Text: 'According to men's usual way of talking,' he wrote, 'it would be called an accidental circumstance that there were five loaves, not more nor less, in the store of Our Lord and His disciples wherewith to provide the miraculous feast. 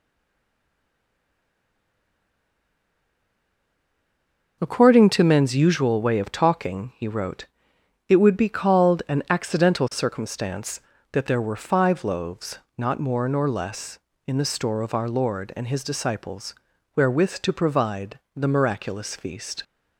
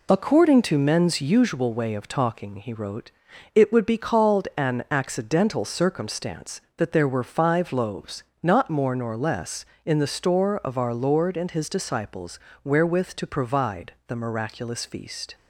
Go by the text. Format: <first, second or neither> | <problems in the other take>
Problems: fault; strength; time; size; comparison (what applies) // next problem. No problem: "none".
second | stays silent before the first word; strong; until 4.6 s; 4.6 s long // pauses between "disciples" and "wherewith"; at 16.5 s; 0.42 s long; slight in the second // pauses between "provide" and "the"; slight; at 18.1 s; 0.16 s long